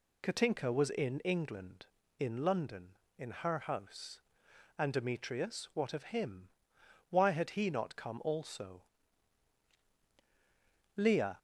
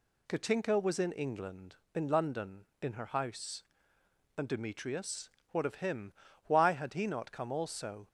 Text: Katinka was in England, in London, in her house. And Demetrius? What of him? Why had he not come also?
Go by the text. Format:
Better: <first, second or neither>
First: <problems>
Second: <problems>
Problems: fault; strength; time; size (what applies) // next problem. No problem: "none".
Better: second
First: goes on to say "Leah"; slight; from 10.9 s on; 0.42 s long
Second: none